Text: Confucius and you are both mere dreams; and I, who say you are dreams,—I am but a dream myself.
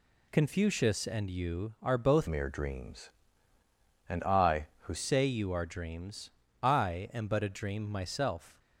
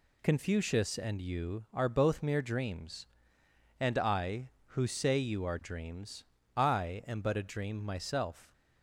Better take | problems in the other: second | changes voice from "mere" to "who"; from 2.2 to 4.9 s; 2.7 s long

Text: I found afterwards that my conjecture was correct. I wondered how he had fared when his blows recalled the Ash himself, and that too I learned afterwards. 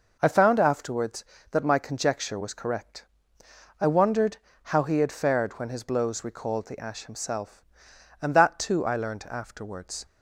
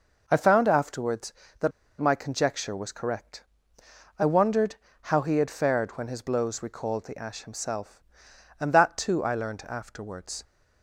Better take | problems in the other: first | pauses between "that" and "my"; slight; at 1.7 s; 0.28 s long // pauses between "wondered" and "how"; slight; at 4.7 s; 0.26 s long; slight in the first

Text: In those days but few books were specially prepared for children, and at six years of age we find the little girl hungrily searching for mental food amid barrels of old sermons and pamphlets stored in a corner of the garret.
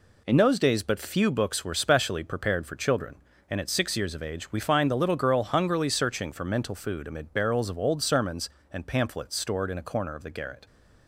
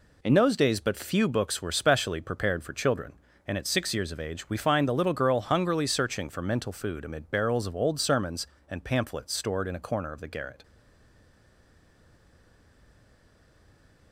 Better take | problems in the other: first | stays silent after the last word; strong; from 10.6 s on; 3.5 s long

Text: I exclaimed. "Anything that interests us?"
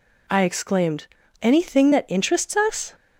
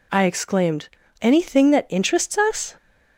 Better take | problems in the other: neither | none

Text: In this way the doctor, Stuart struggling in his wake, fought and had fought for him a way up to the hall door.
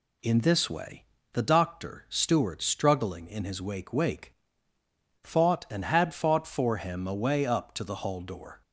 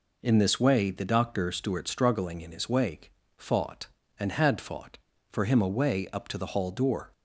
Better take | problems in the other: second | pauses between "way" and "the"; slight; at 1.0 s; 0.28 s long // says "wake" twice; at 3.9 s

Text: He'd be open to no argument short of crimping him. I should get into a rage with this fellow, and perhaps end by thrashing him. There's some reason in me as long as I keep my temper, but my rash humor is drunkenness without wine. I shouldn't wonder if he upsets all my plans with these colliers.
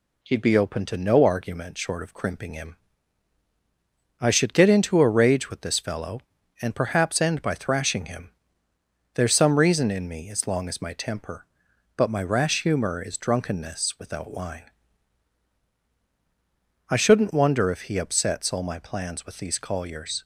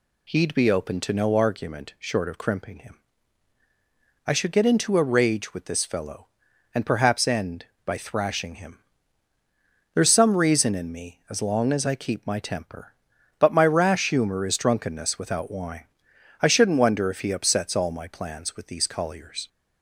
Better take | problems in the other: second | skips "I keep"; at 10.8 s

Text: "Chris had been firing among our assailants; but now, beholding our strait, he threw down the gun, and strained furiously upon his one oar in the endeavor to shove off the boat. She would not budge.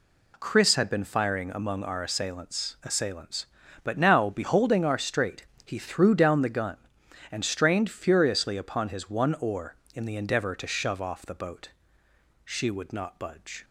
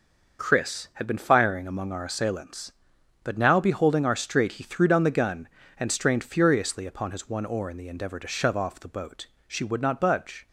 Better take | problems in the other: second | says "assailants" twice; at 2.8 s

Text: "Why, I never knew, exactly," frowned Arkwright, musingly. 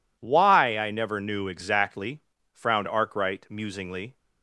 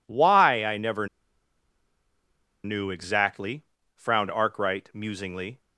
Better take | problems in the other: first | pauses between "never" and "knew"; strong; at 1.0 s; 1.5 s long

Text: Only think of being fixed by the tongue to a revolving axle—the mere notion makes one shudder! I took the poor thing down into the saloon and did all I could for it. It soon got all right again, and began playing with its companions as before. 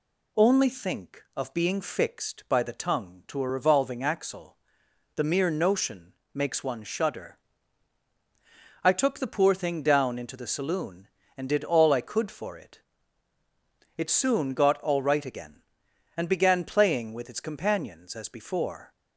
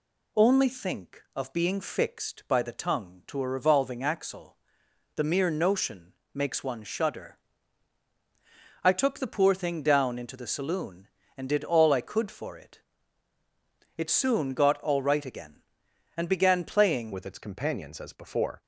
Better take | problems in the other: first | pauses between "notion" and "makes"; slight; at 6.1 s; 0.24 s long; slight in the first // changes voice at "with"; from 17.1 s on; 1.5 s long

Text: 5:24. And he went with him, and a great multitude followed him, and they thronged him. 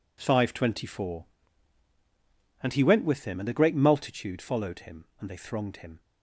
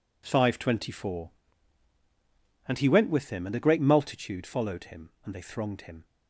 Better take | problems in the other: neither | none

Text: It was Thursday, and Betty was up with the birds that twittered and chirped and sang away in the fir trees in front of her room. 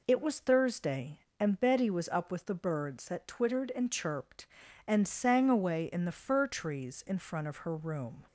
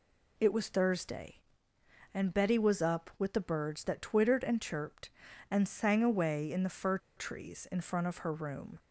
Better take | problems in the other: first | pauses between "fir" and "trees"; slight; at 6.9 s; 0.19 s long

